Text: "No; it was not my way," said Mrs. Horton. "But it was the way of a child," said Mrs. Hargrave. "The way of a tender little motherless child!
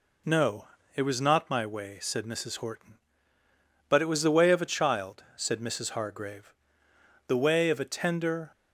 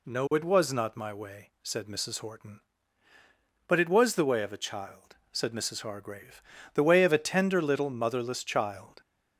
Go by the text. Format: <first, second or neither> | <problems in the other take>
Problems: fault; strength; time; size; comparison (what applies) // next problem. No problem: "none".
second | stops before "little motherless child"; at 8.5 s